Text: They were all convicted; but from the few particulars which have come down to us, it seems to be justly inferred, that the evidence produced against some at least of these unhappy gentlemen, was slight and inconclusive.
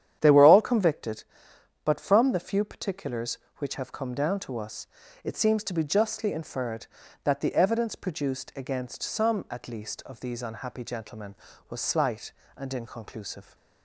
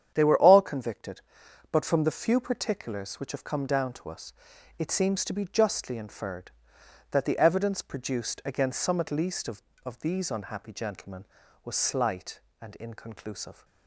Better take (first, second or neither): first